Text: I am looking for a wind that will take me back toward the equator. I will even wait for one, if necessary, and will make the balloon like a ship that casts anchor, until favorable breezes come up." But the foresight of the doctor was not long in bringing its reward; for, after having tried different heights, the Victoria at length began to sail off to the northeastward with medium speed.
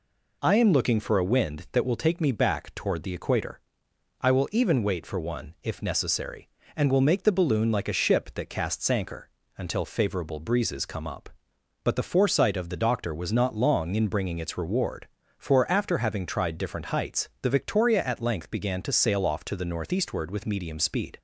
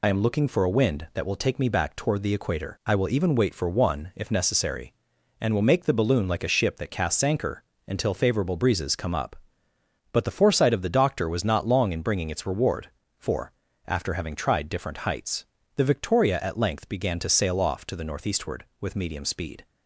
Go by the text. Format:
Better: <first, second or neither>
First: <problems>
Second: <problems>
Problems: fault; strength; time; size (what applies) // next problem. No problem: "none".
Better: first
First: none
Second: loses the start of "I"; at 0.0 s; 55 ms